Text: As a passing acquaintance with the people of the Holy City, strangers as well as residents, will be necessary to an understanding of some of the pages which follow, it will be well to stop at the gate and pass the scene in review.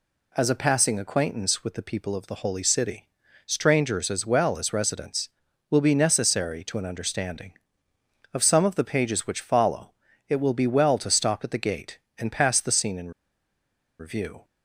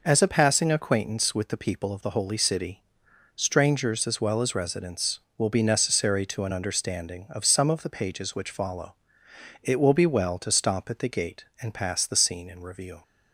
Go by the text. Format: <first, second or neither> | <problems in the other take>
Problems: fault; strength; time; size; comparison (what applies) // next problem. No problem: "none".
second | pauses between "in" and "review"; noticeable; at 13.0 s; 0.89 s long